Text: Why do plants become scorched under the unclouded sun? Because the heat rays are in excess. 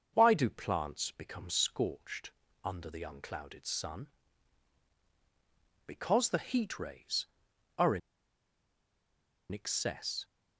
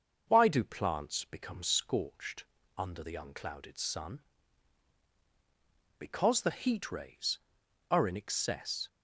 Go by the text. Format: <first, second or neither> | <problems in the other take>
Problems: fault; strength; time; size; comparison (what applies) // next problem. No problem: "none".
second | starts louder than the rest; until 1.1 s; 6 dB; also in the second // pauses between "scorched" and "under"; slight; at 2.3 s; 0.32 s long; slight in the second // pauses between "in" and "excess"; strong; at 8.0 s; 1.5 s long